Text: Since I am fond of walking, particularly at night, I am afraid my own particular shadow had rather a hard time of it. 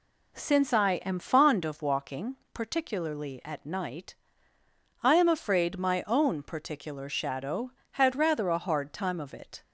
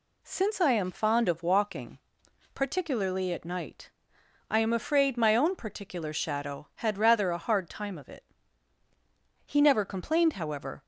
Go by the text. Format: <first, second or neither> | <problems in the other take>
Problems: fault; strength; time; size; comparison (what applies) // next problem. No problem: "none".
first | goes on to say "He never complained however"; from 9.4 s on; 1.3 s long